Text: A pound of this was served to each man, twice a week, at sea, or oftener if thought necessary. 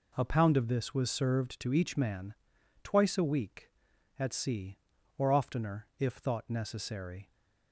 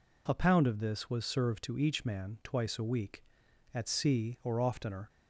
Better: first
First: none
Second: stops before "if thought necessary"; at 5.0 s

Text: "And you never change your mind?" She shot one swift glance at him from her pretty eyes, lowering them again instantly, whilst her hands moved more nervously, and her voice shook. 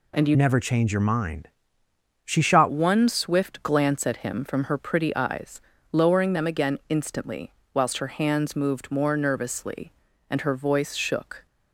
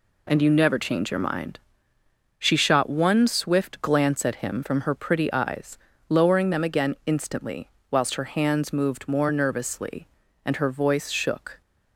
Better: second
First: changes voice from "never" to "shot"; from 0.3 to 2.6 s; 2.3 s long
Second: none

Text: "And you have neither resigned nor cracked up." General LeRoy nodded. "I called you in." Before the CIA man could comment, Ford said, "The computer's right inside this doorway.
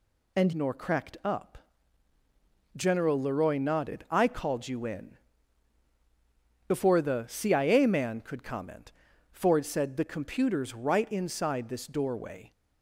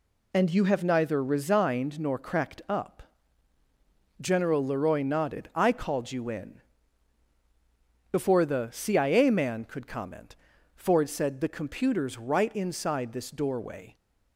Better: second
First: skips "you have neither resigned"; at 0.5 s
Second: none

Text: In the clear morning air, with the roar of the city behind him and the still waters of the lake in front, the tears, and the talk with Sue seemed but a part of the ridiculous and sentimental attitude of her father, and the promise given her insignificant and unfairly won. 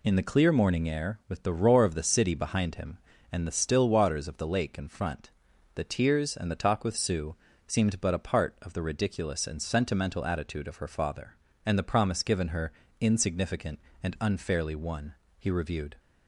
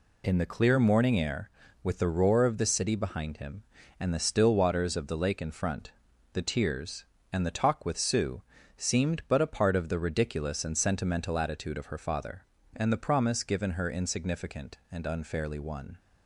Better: second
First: pauses between "Sue" and "seemed"; slight; at 7.3 s; 0.32 s long // pauses between "her" and "insignificant"; slight; at 12.7 s; 0.30 s long // goes on to say "He reviewed"; from 15.3 s on; 0.58 s long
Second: pauses between "Sue" and "seemed"; slight; at 8.4 s; 0.34 s long

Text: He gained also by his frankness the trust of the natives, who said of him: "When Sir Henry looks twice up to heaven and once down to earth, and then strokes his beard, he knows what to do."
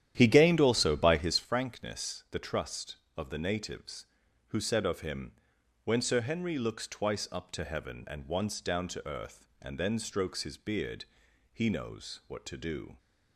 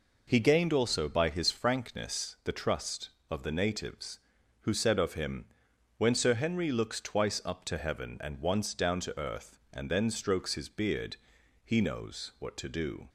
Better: second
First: starts louder than the rest; strong; until 1.5 s; 11 dB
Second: none

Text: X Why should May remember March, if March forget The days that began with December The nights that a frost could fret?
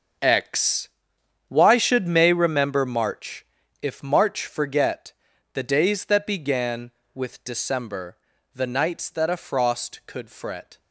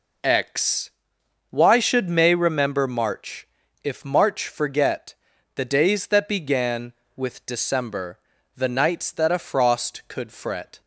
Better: second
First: gets quieter; strong; throughout; 12 dB // pauses between "X" and "Why"; noticeable; at 0.8 s; 0.58 s long // pauses between "forget" and "The"; at 5.1 s; 0.40 s long // pauses between "December" and "The"; slight; at 8.1 s; 0.36 s long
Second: pauses between "X" and "Why"; noticeable; at 0.9 s; 0.58 s long // pauses between "forget" and "The"; at 5.1 s; 0.40 s long // pauses between "December" and "The"; slight; at 8.1 s; 0.36 s long

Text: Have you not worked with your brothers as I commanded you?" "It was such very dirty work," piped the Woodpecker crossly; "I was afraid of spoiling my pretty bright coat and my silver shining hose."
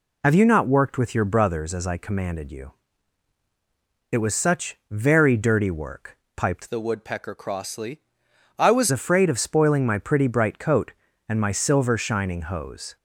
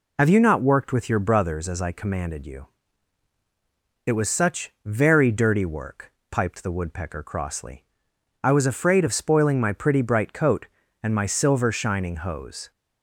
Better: second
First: changes voice from "the" to "was"; from 6.6 to 8.9 s; 2.3 s long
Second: none

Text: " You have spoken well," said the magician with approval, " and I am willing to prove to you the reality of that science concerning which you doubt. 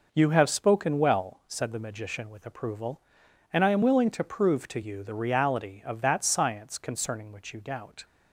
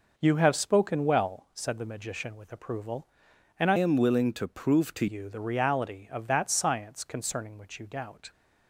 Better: first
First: none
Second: changes voice from "am" to "to"; from 3.7 to 5.0 s; 1.3 s long

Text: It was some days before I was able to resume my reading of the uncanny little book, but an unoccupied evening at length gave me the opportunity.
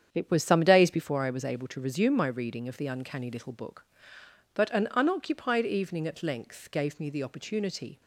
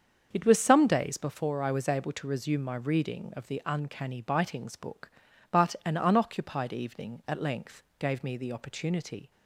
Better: first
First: starts louder than the rest; strong; until 1.1 s; 8.5 dB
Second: starts louder than the rest; until 1.3 s; 7 dB // says "bitings" for "little"; at 4.2 s // pauses between "length" and "gave"; slight; at 7.8 s; 0.16 s long

